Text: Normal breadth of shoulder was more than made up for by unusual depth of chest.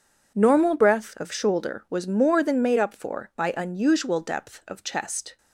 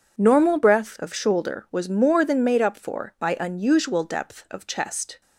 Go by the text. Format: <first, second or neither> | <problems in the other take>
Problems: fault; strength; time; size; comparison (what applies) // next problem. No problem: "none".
neither | none